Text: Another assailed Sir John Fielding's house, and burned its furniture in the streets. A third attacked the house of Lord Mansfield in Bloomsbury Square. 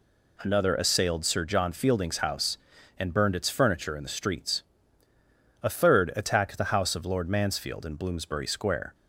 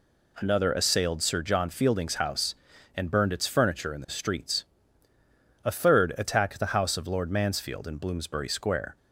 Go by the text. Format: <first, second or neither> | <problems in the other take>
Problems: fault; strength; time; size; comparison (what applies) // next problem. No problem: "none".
neither | none